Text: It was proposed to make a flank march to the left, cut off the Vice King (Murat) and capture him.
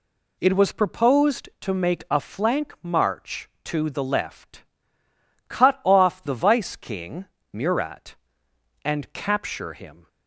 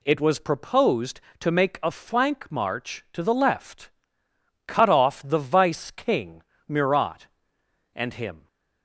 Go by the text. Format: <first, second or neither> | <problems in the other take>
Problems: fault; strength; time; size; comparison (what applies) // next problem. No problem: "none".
first | skips "capture"; at 8.1 s